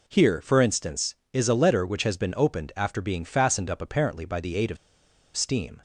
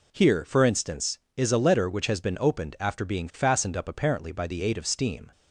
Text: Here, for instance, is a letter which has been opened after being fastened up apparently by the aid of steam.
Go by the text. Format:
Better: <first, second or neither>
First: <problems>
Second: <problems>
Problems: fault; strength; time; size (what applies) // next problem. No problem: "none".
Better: second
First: pauses between "of" and "steam"; noticeable; at 4.7 s; 0.58 s long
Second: none